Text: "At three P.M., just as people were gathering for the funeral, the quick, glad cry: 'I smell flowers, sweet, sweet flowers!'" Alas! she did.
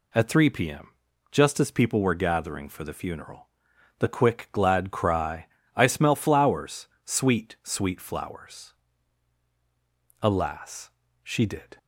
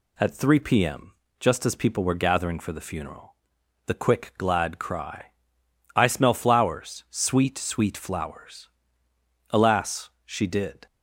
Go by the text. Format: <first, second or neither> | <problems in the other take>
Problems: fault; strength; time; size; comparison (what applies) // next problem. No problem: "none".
neither | none